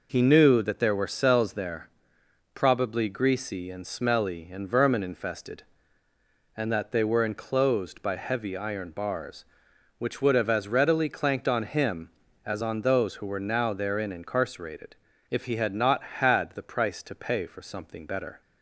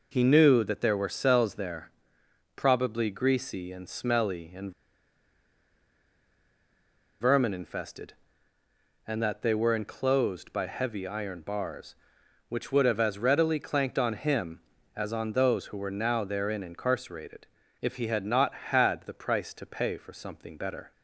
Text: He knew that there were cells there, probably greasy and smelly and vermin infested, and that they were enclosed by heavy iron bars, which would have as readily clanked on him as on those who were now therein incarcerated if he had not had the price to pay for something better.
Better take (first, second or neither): first